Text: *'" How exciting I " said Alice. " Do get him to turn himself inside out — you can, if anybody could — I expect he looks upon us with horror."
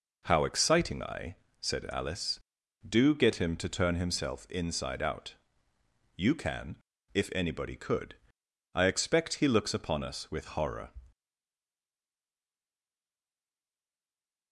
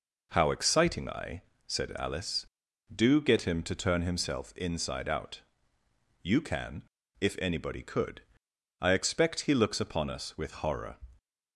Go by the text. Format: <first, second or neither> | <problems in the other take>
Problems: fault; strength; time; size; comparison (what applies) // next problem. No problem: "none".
second | stays silent after the last word; strong; from 11.1 s on; 3.4 s long